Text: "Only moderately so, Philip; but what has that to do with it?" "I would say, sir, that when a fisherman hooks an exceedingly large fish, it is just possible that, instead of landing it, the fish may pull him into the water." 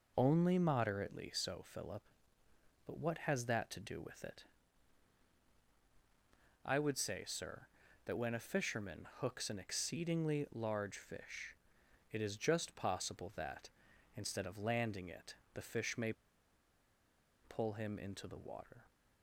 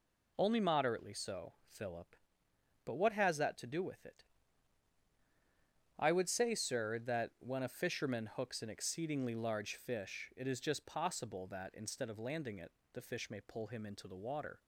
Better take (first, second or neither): second